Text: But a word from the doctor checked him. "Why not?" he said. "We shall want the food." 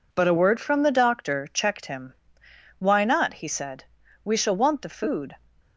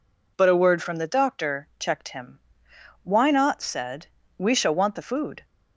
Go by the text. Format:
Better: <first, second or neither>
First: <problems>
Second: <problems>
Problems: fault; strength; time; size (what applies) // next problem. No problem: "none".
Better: first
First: none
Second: skips "he"; at 3.6 s